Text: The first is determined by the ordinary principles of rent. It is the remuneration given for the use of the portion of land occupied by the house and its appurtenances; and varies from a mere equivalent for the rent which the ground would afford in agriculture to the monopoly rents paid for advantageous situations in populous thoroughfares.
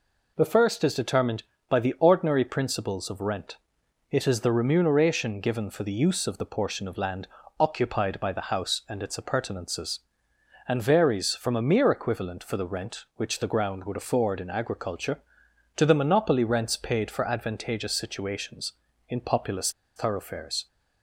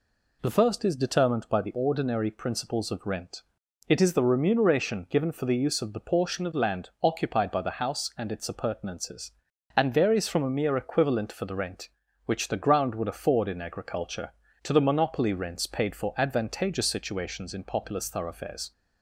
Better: second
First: pauses between "land" and "occupied"; slight; at 7.2 s; 0.32 s long // pauses between "populous" and "thoroughfares"; slight; at 19.6 s; 0.26 s long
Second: none

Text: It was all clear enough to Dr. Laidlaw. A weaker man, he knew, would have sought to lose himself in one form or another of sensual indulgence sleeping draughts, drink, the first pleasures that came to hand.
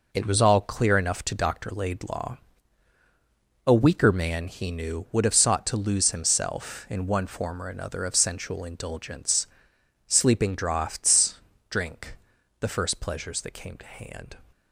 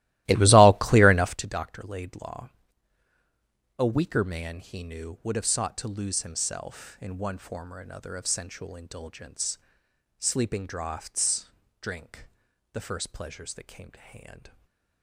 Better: first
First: pauses between "indulgence" and "sleeping"; noticeable; at 9.4 s; 0.62 s long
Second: starts louder than the rest; strong; until 1.5 s; 16 dB // pauses between "indulgence" and "sleeping"; noticeable; at 9.5 s; 0.62 s long // stays silent after the last word; slight; from 14.4 s on; 0.6 s long

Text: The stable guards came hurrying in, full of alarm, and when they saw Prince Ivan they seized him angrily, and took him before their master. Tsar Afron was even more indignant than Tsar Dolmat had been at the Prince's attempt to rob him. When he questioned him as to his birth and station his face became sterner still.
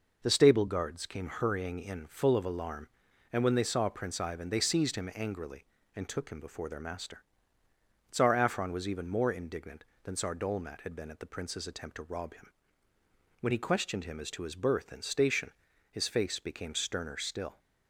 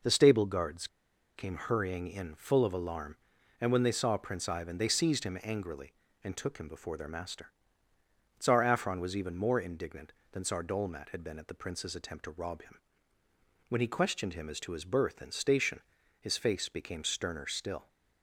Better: first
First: pauses between "station" and "his"; at 15.5 s; 0.40 s long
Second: pauses between "guards" and "came"; noticeable; at 0.8 s; 0.50 s long // pauses between "station" and "his"; at 15.7 s; 0.40 s long

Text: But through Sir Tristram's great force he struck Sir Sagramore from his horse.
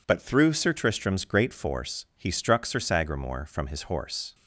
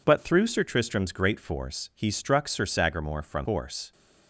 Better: first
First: none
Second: skips "his"; at 3.4 s

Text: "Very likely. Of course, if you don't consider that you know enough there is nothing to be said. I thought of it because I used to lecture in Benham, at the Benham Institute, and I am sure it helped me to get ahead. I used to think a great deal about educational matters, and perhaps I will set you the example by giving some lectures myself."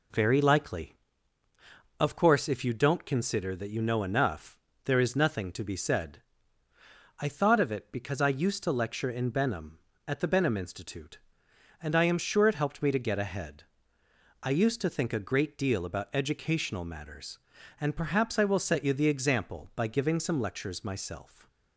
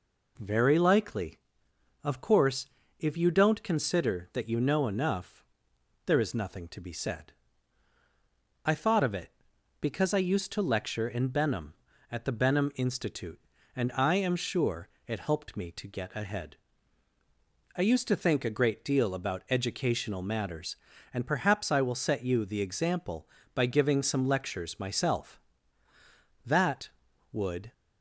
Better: first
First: pauses between "enough" and "there"; slight; at 4.5 s; 0.24 s long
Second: pauses between "enough" and "there"; noticeable; at 5.4 s; 0.62 s long // pauses between "sure" and "it"; slight; at 14.8 s; 0.18 s long // goes on to say "That would"; noticeable; from 26.4 s on; 1.2 s long

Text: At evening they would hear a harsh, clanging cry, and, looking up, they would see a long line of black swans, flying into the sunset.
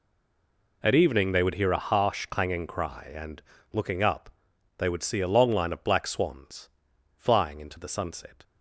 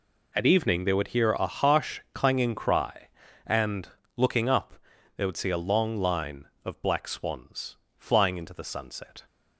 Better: second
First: stays silent before the first word; slight; until 0.8 s; 0.8 s long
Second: none

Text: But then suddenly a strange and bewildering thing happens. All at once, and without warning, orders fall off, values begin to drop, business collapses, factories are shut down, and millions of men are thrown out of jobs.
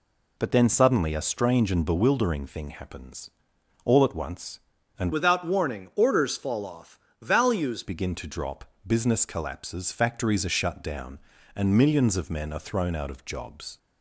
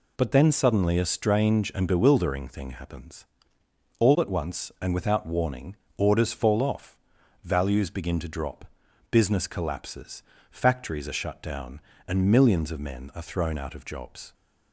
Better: second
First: changes voice from "without" to "values"; from 5.1 to 7.8 s; 2.7 s long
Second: none

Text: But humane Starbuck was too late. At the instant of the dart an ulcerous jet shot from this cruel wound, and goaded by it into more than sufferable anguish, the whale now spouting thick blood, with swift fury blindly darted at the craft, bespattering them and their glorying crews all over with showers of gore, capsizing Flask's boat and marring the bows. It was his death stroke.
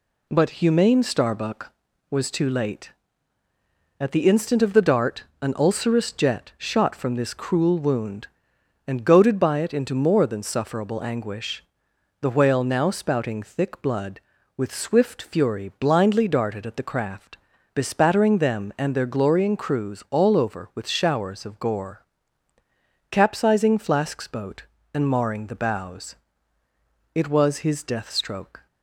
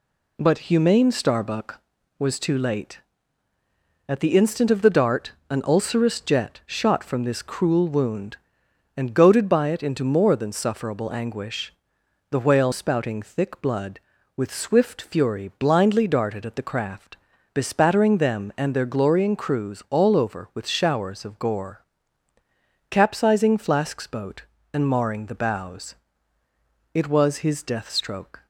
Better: first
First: pauses between "dart" and "an"; slight; at 5.2 s; 0.18 s long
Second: pauses between "dart" and "an"; slight; at 5.3 s; 0.18 s long // skips "now"; at 12.7 s

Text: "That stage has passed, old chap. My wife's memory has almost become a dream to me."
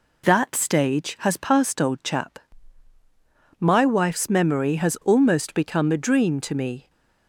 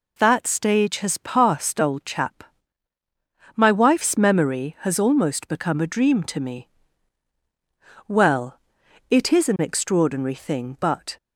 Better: first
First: none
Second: goes on to say "Well it is an extraordinary thing but"; strong; from 8.0 s on; 3.0 s long

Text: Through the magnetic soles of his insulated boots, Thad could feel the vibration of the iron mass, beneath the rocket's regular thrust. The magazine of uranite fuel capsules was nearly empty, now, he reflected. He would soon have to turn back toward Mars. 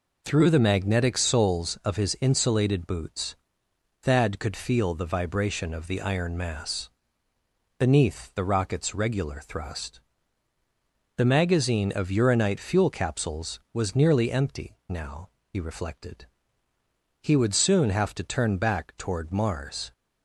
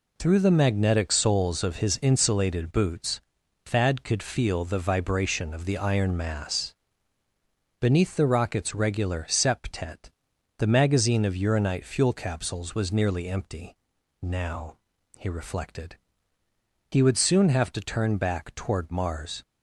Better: first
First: none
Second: says "septet" for "thrust"; at 9.2 s

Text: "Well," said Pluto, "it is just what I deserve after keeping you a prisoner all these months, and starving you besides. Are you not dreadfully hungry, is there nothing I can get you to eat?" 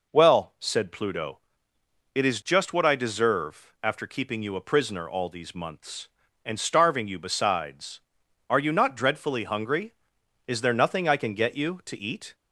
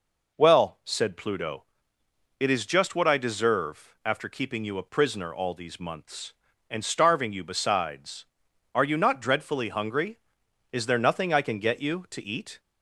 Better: neither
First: none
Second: none

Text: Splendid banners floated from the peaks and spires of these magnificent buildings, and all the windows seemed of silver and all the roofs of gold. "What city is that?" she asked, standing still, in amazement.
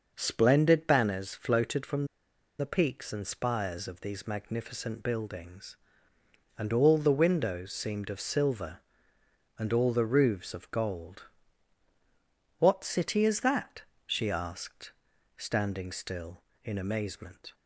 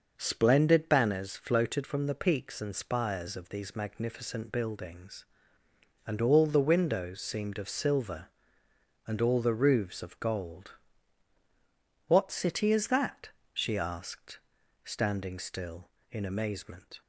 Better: second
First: pauses between "from" and "the"; noticeable; at 2.0 s; 0.53 s long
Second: none

